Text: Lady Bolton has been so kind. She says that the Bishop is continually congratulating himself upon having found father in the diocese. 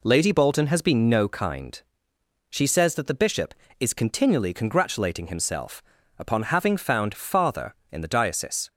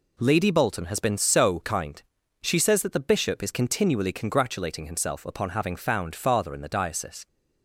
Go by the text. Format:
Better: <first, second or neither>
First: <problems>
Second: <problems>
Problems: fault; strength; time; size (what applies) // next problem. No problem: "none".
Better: second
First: says "no" for "so"; at 1.1 s // pauses between "himself" and "upon"; slight; at 5.8 s; 0.36 s long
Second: none